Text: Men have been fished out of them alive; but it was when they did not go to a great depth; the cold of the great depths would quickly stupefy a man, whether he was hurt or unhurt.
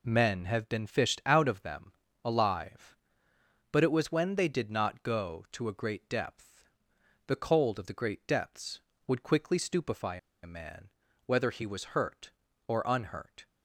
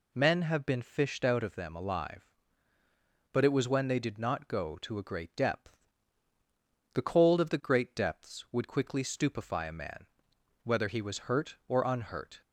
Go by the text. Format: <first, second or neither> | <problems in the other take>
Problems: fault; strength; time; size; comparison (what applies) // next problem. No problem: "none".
second | pauses between "them" and "alive"; slight; at 1.9 s; 0.32 s long // pauses between "stupefy" and "a"; slight; at 10.1 s; 0.25 s long